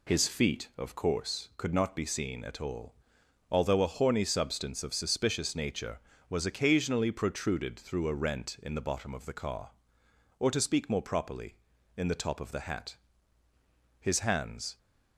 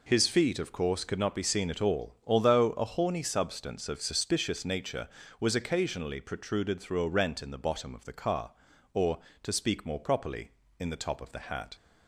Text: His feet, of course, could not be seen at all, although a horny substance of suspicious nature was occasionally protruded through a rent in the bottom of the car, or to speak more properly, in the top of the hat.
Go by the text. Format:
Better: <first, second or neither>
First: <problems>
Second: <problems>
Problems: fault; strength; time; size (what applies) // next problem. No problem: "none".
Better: second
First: goes on to say "His hands"; noticeable; from 13.9 s on; 0.78 s long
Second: none